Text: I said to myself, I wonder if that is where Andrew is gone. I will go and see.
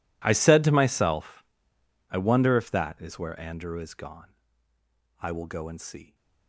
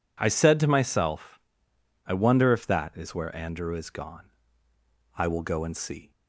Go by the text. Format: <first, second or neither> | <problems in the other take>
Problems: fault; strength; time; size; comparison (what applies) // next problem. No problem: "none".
second | gets quieter; strong; throughout; 21 dB